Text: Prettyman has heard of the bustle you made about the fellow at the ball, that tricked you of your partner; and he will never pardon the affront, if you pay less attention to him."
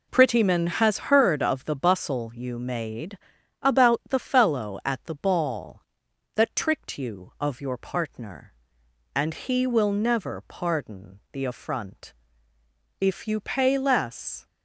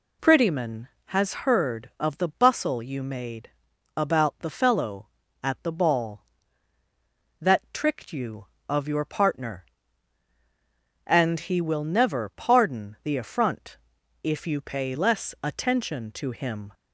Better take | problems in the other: second | pauses between "made" and "about"; at 3.1 s; 0.42 s long; noticeable in the second // stops before "attention to him"; at 14.4 s

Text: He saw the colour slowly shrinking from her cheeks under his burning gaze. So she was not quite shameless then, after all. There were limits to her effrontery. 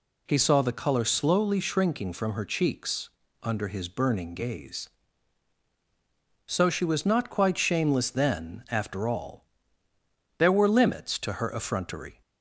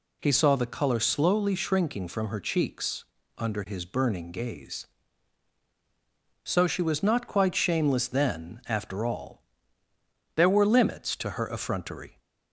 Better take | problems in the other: neither | pauses between "cheeks" and "under"; slight; the same in both

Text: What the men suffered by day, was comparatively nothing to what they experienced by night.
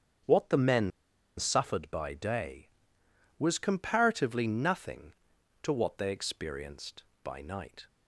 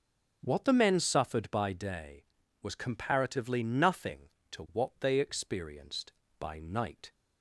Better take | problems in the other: second | starts louder than the rest; strong; until 1.7 s; 8 dB // pauses between "men" and "suffered"; noticeable; at 0.9 s; 0.49 s long

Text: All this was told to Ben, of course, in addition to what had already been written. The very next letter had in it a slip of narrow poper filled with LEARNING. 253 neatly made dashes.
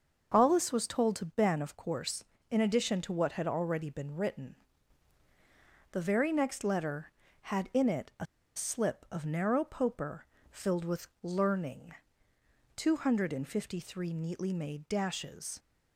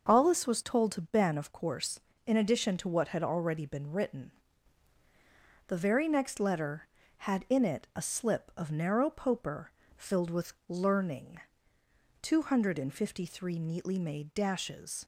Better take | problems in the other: second | starts louder than the rest; until 1.3 s; 6.5 dB; also in the second // pauses between "a" and "slip"; slight; at 8.2 s; 0.31 s long // pauses between "poper" and "filled"; slight; at 10.2 s; 0.28 s long; slight in the second

